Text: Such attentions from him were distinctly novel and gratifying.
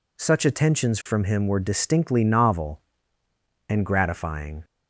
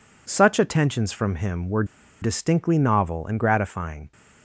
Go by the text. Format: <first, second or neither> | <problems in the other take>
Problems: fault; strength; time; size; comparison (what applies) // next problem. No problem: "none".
first | pauses between "were" and "distinctly"; at 1.8 s; 0.36 s long